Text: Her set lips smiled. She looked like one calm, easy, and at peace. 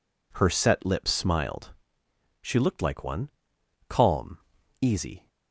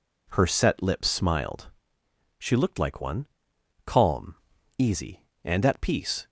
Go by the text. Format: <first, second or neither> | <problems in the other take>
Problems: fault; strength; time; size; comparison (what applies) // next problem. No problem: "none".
second | pauses between "one" and "calm"; noticeable; at 3.2 s; 0.58 s long; noticeable in the second // stops before "and at peace"; at 5.2 s